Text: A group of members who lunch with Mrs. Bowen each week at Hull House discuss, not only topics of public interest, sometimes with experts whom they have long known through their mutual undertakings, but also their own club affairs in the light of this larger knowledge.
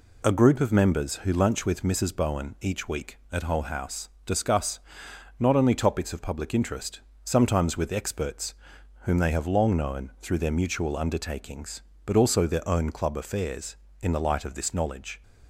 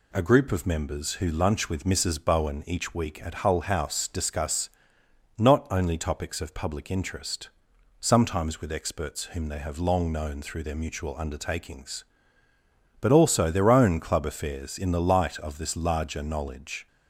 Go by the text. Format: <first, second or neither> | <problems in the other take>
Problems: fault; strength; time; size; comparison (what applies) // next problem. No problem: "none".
second | pauses between "House" and "discuss"; slight; at 4.0 s; 0.16 s long // pauses between "experts" and "whom"; noticeable; at 8.5 s; 0.46 s long // skips "larger"; at 14.7 s